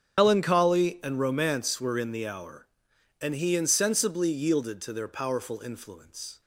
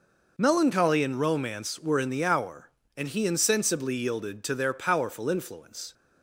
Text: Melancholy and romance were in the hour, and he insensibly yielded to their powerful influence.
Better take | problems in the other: second | loses the start of "Melancholy"; at 0.1 s; 110 ms // starts louder than the rest; strong; until 1.2 s; 8 dB

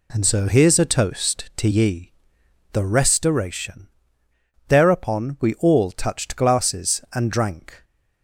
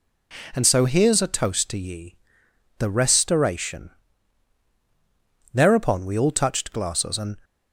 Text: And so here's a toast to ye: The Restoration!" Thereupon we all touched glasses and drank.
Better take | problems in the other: first | stops before "drank"; at 7.4 s

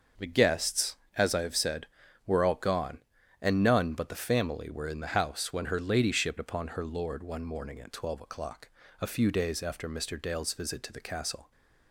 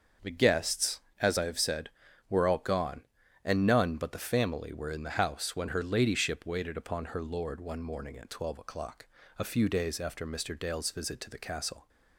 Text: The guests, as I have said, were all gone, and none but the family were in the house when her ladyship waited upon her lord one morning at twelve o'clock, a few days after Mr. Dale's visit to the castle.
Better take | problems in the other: second | starts louder than the rest; until 1.4 s; 6.5 dB; also in the second // skips "waited"; at 6.3 s

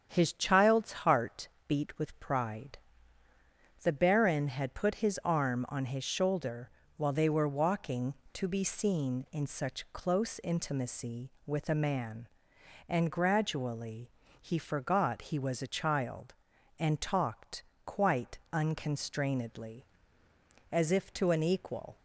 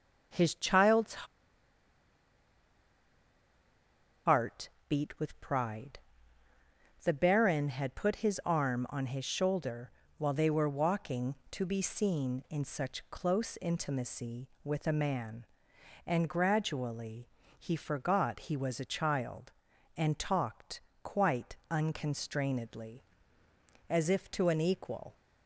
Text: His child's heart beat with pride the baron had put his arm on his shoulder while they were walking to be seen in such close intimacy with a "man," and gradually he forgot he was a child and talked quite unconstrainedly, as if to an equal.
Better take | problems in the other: first | starts louder than the rest; strong; until 4.3 s; 8 dB; strong in the first // pauses between "child's" and "heart"; strong; at 1.2 s; 3.0 s long // pauses between "heart" and "beat"; slight; at 4.6 s; 0.22 s long; slight in the first // pauses between "pride" and "the"; at 5.9 s; 1.0 s long; also in the first // pauses between "shoulder" and "while"; slight; at 9.8 s; 0.28 s long; slight in the first // pauses between "gradually" and "he"; slight; at 17.2 s; 0.28 s long; slight in the first // pauses between "talked" and "quite"; slight; at 20.8 s; 0.22 s long; slight in the first // pauses between "quite" and "unconstrainedly"; slight; at 21.5 s; 0.16 s long; slight in the first

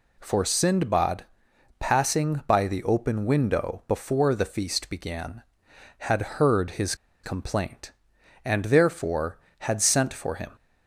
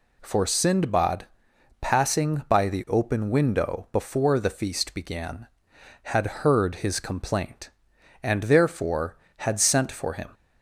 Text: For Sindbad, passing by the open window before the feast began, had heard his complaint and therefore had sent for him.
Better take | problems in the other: second | pauses between "had" and "heard"; slight; at 6.2 s; 0.16 s long; slight in the second // pauses between "his" and "complaint"; slight; at 6.9 s; 0.28 s long

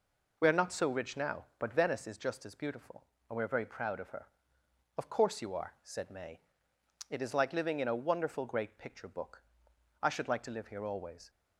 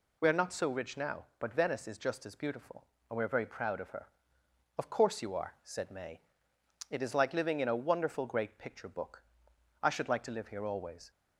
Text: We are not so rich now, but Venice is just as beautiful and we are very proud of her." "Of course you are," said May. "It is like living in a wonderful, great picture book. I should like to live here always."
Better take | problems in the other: second | starts louder than the rest; noticeable; until 2.2 s; 4.5 dB

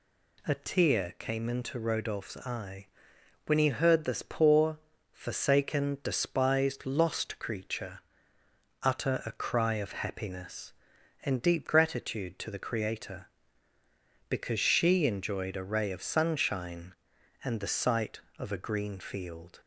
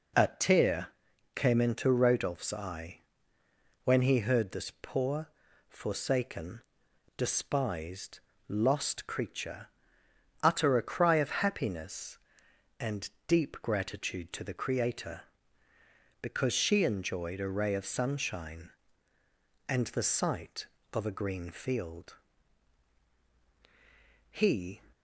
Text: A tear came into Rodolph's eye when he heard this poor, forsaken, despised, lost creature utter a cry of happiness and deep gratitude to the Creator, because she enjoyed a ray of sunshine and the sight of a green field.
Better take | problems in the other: first | pauses between "tear" and "came"; at 0.9 s; 0.44 s long // pauses between "eye" and "when"; noticeable; at 3.0 s; 0.82 s long; noticeable in the first // pauses between "creature" and "utter"; noticeable; at 9.6 s; 0.74 s long; noticeable in the first // pauses between "and" and "deep"; slight; at 13.1 s; 0.16 s long // goes on to say "He"; from 24.3 s on; 0.50 s long

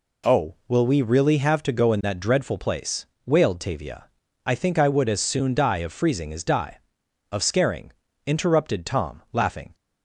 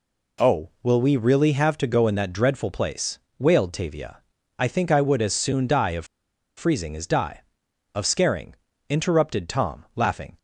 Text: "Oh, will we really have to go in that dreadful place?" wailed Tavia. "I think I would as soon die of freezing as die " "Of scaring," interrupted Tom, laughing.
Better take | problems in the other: first | pauses between "of" and "freezing"; noticeable; at 6.0 s; 0.51 s long

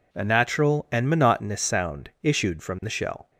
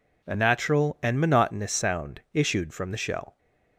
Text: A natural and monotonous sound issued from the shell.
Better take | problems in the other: neither | none

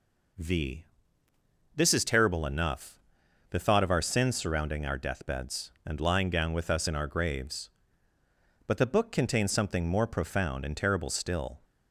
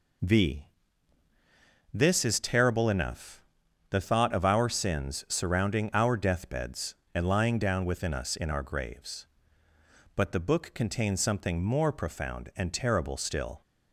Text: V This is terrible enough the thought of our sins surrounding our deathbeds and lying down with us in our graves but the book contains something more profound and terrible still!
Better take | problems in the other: first | pauses between "V" and "This"; strong; at 0.6 s; 1.2 s long; noticeable in the first // pauses between "enough" and "the"; noticeable; at 3.4 s; 0.48 s long; noticeable in the first // says "within" for "with"; at 7.8 s

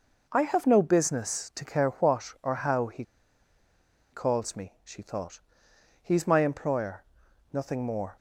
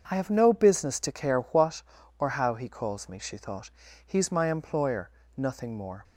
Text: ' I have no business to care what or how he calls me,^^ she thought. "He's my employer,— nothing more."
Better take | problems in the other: second | pauses between "he" and "calls"; at 3.0 s; 1.0 s long

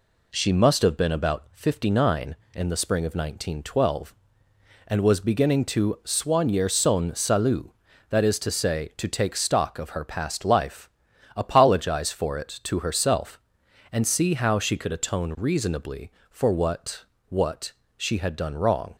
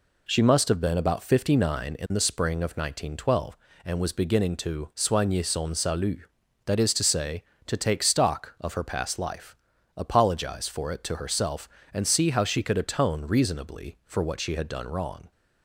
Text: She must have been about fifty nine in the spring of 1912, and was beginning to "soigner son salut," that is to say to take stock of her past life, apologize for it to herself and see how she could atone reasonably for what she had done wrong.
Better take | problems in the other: second | says "what" twice; at 17.2 s

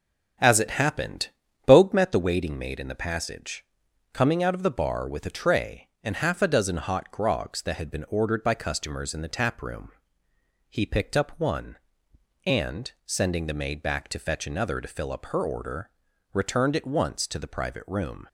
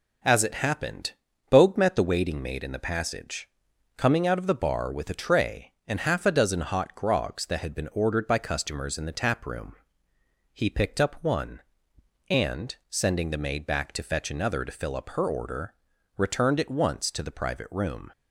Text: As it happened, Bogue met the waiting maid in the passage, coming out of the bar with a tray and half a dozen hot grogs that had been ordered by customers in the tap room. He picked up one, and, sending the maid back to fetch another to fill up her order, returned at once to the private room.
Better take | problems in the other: second | starts louder than the rest; strong; until 2.0 s; 8 dB

